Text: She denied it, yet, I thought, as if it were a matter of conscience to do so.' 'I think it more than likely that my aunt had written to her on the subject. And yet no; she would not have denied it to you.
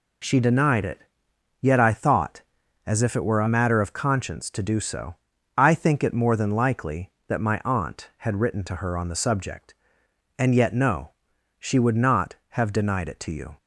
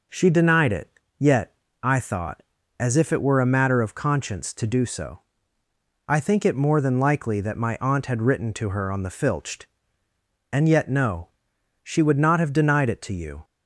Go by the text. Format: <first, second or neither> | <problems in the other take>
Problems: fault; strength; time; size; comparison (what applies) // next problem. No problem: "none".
first | says "filched" for "subject"; at 9.1 s